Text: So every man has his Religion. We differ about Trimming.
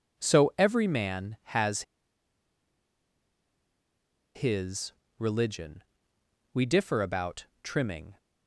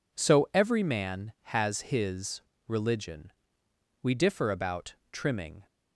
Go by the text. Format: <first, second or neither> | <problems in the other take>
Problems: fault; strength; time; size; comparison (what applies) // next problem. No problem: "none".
second | pauses between "has" and "his"; strong; at 1.8 s; 2.5 s long // pauses between "his" and "Religion"; slight; at 4.9 s; 0.28 s long; slight in the second // pauses between "about" and "Trimming"; slight; at 7.4 s; 0.18 s long; slight in the second